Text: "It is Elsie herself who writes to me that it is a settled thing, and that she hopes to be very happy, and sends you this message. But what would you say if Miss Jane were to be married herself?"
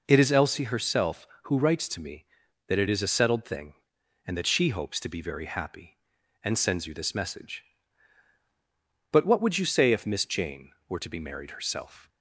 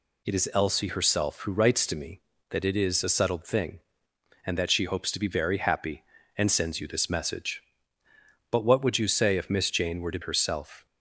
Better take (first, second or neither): first